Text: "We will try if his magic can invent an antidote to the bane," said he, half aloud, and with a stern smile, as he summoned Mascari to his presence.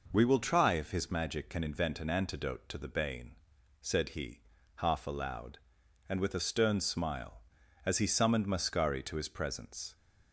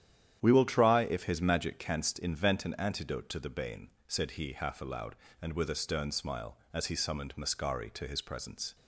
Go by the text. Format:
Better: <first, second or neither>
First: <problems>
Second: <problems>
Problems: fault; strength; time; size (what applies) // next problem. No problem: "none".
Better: first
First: none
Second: starts louder than the rest; strong; until 1.4 s; 10 dB // says "canst" for "can"; at 1.7 s